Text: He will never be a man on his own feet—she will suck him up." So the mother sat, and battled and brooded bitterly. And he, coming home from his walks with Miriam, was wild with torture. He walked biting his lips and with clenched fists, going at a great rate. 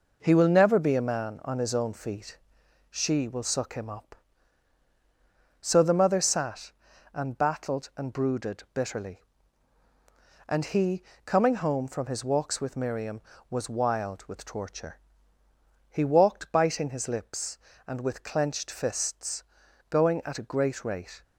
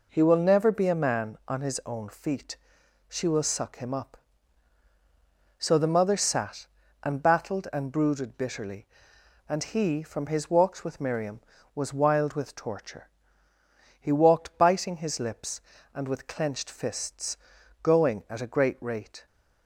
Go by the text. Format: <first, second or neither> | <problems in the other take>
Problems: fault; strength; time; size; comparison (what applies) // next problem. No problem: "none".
first | skips "coming home"; at 10.0 s